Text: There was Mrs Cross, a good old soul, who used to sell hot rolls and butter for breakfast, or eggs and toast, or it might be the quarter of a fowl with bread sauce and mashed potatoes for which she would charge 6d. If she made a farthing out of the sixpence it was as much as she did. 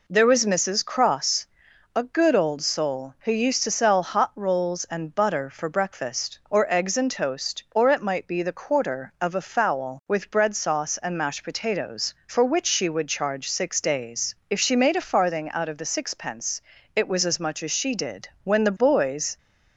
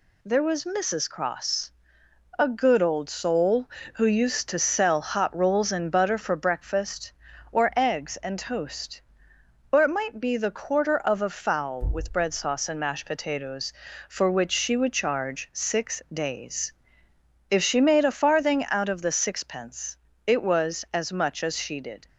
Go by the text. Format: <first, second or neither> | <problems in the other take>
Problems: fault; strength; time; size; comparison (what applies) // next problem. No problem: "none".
second | pauses between "sixpence" and "it"; slight; at 16.6 s; 0.36 s long; slight in the second // goes on to say "When the boys"; noticeable; from 18.4 s on; 0.94 s long